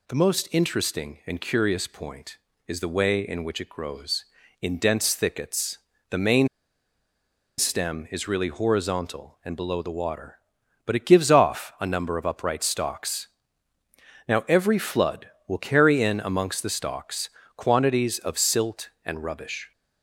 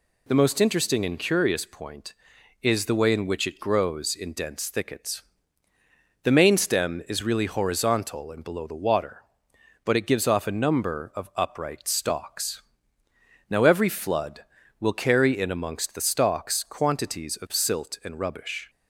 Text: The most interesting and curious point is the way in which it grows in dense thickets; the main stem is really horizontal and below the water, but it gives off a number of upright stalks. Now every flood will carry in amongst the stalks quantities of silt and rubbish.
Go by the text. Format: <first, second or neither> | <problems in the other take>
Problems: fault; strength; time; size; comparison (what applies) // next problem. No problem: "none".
second | pauses between "main" and "stem"; at 6.4 s; 1.1 s long // pauses between "stalks" and "quantities"; slight; at 17.2 s; 0.26 s long